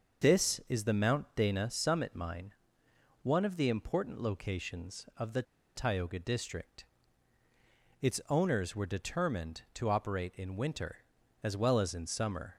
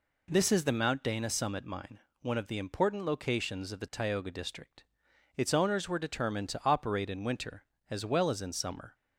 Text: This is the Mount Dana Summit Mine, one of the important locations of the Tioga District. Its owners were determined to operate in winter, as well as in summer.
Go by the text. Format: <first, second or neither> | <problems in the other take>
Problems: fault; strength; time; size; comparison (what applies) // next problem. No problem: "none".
second | starts louder than the rest; until 1.4 s; 6.5 dB // pauses between "the" and "Tioga"; slight; at 5.4 s; 0.32 s long